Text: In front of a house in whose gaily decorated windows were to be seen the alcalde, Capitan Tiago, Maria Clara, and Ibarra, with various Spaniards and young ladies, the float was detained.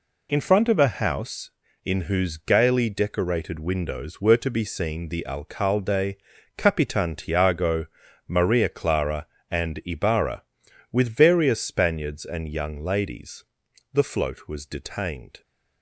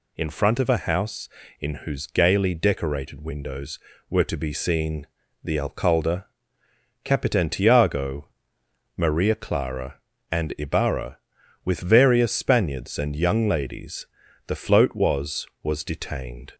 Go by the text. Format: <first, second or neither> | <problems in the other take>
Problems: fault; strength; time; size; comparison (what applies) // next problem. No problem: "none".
first | pauses between "seen" and "the"; at 5.0 s; 0.38 s long // says "was" twice; at 15.6 s